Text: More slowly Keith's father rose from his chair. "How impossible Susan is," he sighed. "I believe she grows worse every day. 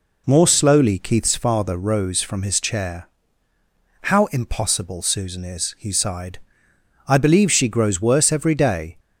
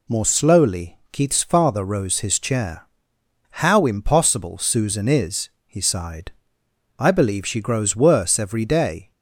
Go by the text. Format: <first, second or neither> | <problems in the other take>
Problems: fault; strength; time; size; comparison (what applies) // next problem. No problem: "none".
first | skips "from"; at 2.1 s